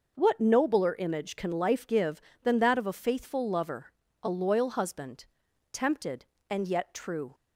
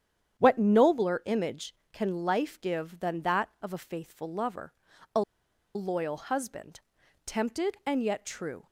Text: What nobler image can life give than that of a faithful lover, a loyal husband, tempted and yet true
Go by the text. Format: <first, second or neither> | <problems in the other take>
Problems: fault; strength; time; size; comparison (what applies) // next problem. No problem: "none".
first | starts louder than the rest; strong; until 1.4 s; 9 dB // pauses between "a" and "loyal"; noticeable; at 5.2 s; 0.54 s long